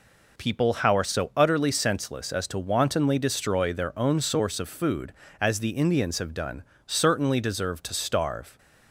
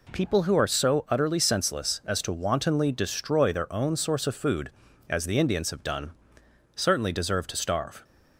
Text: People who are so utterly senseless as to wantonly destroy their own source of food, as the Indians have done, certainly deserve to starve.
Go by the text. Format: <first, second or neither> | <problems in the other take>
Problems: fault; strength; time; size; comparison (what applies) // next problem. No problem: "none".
second | says "how" for "who"; at 0.7 s